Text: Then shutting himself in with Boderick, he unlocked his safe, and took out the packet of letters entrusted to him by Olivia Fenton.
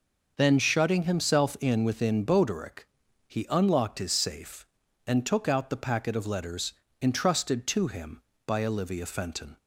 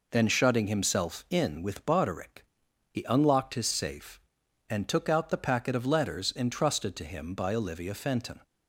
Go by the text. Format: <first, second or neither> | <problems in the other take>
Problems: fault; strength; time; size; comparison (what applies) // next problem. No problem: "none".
second | says "within" for "with"; at 1.8 s // pauses between "letters" and "entrusted"; slight; at 6.7 s; 0.28 s long